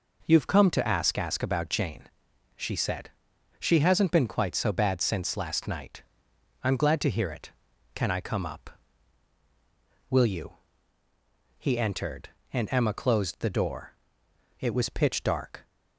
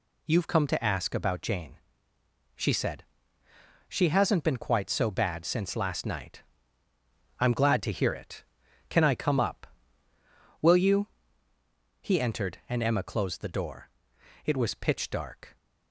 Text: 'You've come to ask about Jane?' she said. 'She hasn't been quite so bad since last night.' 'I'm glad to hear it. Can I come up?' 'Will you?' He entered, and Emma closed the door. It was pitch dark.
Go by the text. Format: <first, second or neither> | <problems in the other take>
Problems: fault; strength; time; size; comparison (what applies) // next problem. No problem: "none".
second | says "ask" twice; at 1.1 s